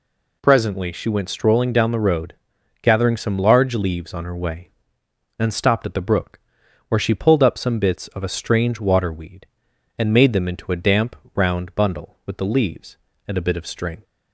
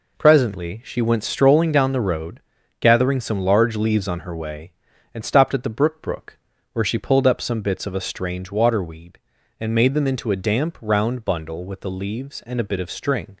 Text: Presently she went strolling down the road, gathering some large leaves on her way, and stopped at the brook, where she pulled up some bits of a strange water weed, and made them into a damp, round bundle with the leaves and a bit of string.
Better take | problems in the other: first | says "brook" twice; at 6.0 s

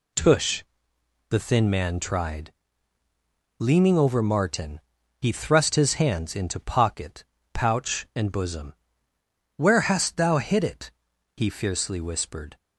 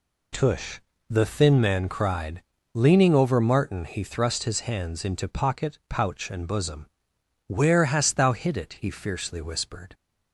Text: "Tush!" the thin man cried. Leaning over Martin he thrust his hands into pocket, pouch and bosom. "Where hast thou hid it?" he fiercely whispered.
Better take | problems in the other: second | says "tried" for "cried"; at 1.9 s // pauses between "Martin" and "he"; at 4.7 s; 0.40 s long

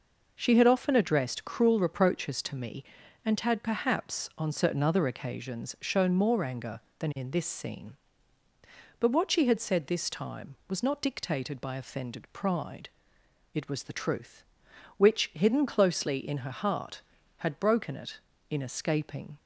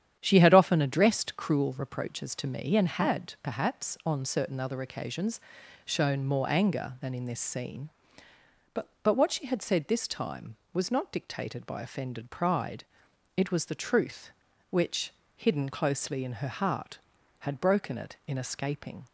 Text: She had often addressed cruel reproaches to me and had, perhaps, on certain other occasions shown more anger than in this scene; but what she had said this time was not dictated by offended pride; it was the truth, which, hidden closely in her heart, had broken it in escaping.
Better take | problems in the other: first | starts louder than the rest; strong; until 1.2 s; 9.5 dB // pauses between "occasions" and "shown"; at 5.3 s; 0.44 s long // says "but" twice; at 9.0 s

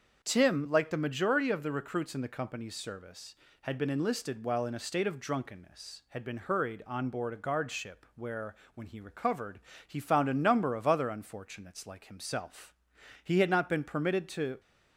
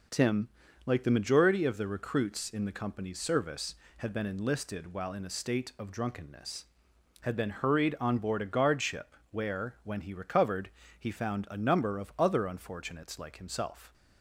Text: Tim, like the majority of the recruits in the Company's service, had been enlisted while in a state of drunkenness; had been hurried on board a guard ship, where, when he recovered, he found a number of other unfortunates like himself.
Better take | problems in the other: second | starts louder than the rest; until 1.2 s; 6.5 dB // goes on to say "He had not been permitted to"; from 13.2 s on; 1.3 s long

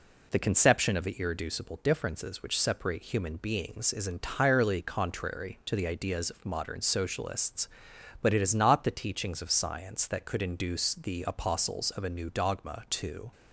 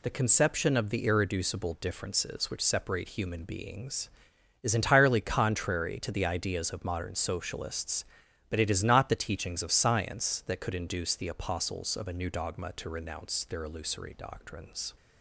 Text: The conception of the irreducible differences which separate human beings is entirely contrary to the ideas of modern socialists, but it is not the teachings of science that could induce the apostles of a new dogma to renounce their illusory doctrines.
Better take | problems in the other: second | stops before "renounce their illusory doctrines"; at 13.3 s

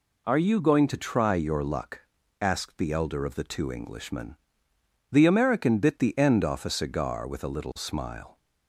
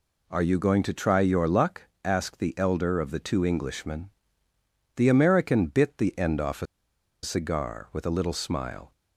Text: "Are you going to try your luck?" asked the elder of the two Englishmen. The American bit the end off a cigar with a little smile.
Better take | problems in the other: first | pauses between "a" and "cigar"; noticeable; at 6.6 s; 0.57 s long

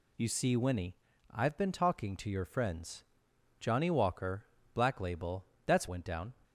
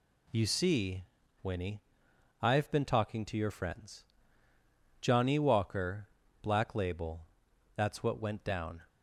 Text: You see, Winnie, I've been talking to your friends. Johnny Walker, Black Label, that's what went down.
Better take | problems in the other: second | skips "what"; at 5.8 s

